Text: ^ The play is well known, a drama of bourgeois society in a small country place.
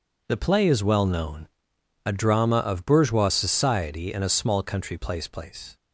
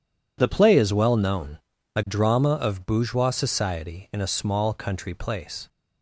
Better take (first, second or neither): second